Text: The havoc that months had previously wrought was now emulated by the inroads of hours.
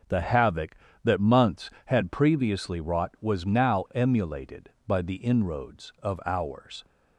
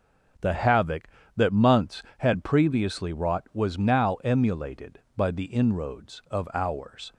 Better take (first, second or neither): neither